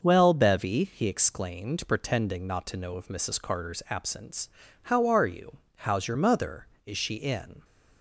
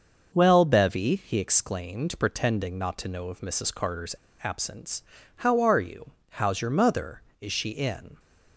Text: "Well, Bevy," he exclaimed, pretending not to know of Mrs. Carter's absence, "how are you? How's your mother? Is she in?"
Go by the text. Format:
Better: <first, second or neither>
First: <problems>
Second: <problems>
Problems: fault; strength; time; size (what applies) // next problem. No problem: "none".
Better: first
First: starts louder than the rest; noticeable; until 1.0 s; 6 dB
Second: starts louder than the rest; until 1.3 s; 6 dB // pauses between "Carter's" and "absence"; slight; at 4.1 s; 0.26 s long